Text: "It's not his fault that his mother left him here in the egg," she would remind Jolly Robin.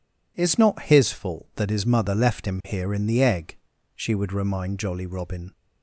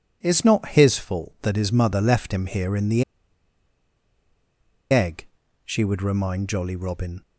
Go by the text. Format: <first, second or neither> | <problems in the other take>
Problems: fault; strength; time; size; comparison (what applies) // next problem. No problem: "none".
first | pauses between "the" and "egg"; strong; at 3.0 s; 1.8 s long